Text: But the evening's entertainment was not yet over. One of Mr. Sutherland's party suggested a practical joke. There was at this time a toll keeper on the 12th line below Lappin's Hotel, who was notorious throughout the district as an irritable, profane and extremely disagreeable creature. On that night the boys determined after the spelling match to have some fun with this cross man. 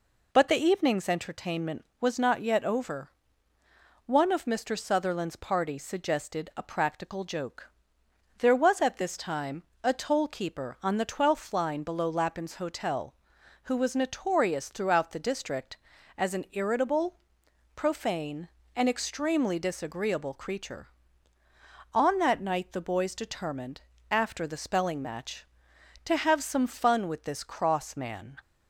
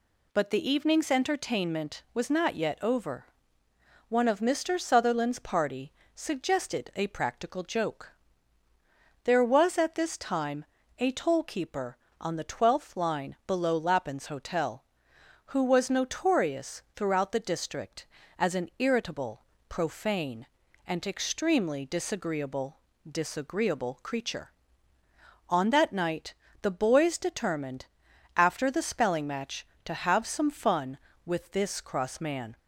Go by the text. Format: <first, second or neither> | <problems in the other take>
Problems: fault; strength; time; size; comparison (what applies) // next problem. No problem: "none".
first | pauses between "party" and "suggested"; slight; at 5.9 s; 0.22 s long // pauses between "time" and "a"; slight; at 10.6 s; 0.34 s long; slight in the first // says "disagreeable" twice; at 23.0 s // pauses between "night" and "the"; slight; at 26.3 s; 0.26 s long // pauses between "determined" and "after"; noticeable; at 27.8 s; 0.50 s long; slight in the first